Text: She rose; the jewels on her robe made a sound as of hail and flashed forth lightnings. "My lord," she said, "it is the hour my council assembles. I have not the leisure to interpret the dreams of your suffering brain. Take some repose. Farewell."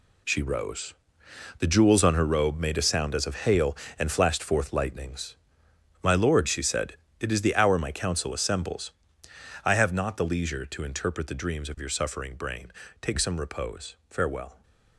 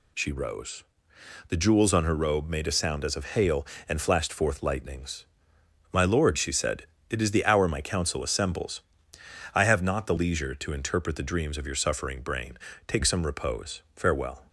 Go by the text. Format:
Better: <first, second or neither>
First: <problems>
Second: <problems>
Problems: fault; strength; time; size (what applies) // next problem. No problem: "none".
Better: second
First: gets quieter; strong; throughout; 10 dB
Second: none